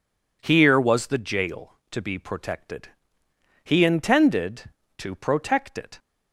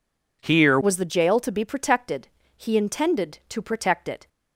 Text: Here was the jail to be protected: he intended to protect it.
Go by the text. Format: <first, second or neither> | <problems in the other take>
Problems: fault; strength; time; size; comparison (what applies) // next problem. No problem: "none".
first | changes voice at "was"; from 0.8 s on; 3.4 s long